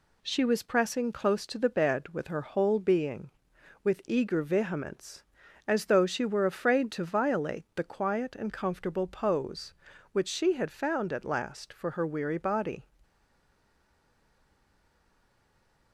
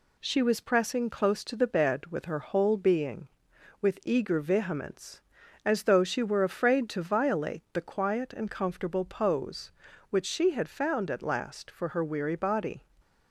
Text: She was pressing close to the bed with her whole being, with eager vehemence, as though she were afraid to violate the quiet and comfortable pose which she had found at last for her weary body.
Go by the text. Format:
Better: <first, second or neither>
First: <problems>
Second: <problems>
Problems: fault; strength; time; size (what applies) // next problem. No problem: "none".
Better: second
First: stays silent after the last word; strong; from 13.0 s on; 2.9 s long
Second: none